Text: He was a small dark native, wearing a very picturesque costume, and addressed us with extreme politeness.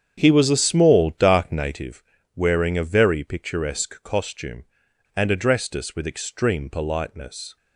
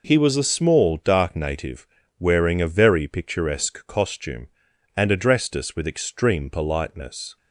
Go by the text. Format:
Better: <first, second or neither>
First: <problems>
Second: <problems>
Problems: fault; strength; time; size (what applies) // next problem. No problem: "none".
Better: second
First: starts louder than the rest; strong; until 1.8 s; 8 dB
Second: none